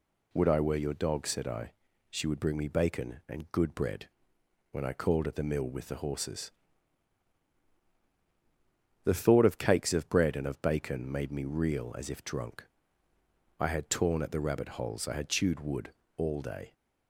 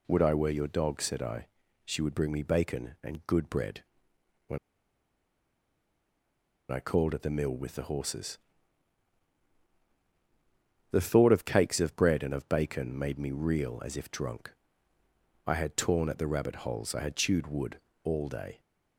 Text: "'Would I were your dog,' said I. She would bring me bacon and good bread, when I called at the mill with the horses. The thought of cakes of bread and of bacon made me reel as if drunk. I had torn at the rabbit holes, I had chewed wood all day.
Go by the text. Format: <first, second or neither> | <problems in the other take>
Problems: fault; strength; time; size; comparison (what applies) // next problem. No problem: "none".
first | pauses between "when" and "I"; strong; at 4.5 s; 2.1 s long // pauses between "wood" and "all"; slight; at 17.7 s; 0.26 s long; slight in the first